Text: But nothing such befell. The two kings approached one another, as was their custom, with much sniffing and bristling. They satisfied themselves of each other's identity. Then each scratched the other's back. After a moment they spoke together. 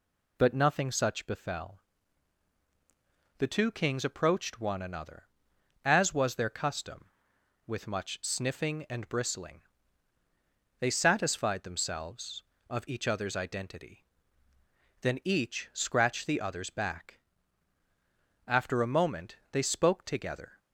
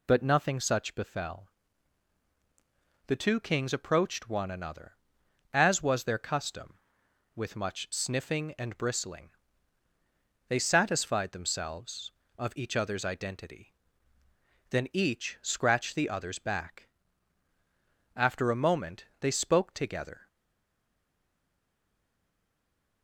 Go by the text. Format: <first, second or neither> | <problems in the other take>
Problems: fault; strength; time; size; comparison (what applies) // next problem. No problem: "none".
first | pauses between "moment" and "they"; slight; at 19.0 s; 0.16 s long; slight in the first // stays silent after the last word; strong; from 20.2 s on; 2.8 s long